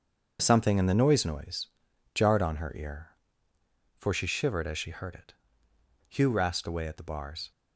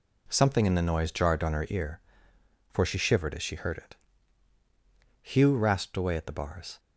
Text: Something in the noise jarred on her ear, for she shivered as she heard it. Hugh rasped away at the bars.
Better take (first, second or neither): second